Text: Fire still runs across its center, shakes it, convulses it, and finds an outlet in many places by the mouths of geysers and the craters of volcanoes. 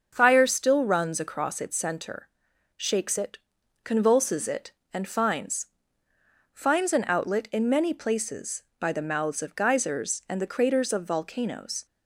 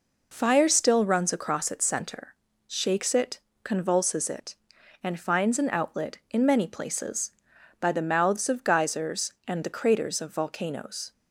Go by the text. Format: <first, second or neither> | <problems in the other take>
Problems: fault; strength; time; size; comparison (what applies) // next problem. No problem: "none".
second | starts louder than the rest; until 1.1 s; 6.5 dB // says "finds" twice; at 6.5 s